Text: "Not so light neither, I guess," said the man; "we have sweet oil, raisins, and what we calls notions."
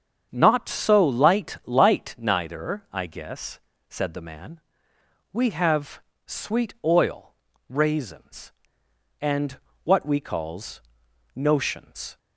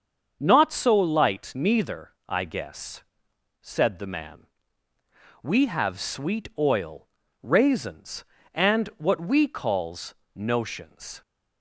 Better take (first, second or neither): second